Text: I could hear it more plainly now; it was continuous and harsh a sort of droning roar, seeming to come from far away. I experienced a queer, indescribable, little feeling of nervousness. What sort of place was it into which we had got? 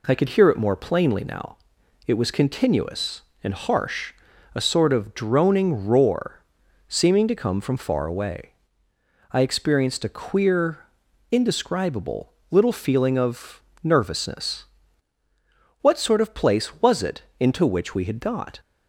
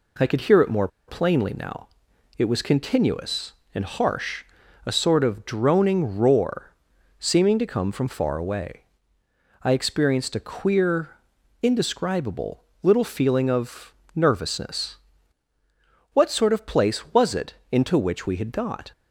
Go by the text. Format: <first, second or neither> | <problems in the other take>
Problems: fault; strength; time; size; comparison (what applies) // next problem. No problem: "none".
first | pauses between "more" and "plainly"; slight; at 0.8 s; 0.20 s long // pauses between "harsh" and "a"; at 4.4 s; 0.42 s long; also in the first // pauses between "of" and "nervousness"; slight; at 13.9 s; 0.18 s long; slight in the first // pauses between "it" and "into"; slight; at 17.5 s; 0.16 s long; slight in the first